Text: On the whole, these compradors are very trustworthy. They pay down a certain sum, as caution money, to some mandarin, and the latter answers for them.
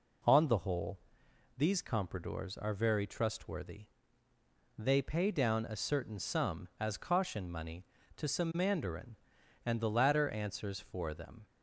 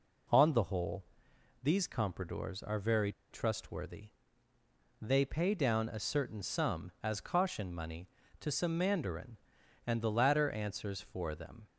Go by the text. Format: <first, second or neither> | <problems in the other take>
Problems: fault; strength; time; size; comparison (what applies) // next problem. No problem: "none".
first | pauses between "very" and "trustworthy"; slight; at 3.1 s; 0.20 s long